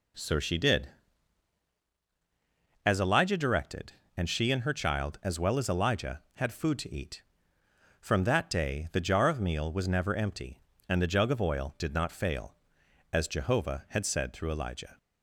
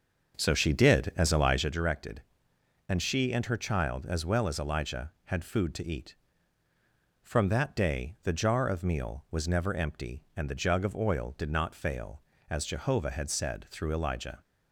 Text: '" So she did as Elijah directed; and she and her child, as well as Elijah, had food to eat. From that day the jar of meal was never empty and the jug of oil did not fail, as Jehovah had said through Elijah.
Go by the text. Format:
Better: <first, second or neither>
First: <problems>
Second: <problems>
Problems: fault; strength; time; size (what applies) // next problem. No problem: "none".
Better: first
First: none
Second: starts louder than the rest; until 1.7 s; 6.5 dB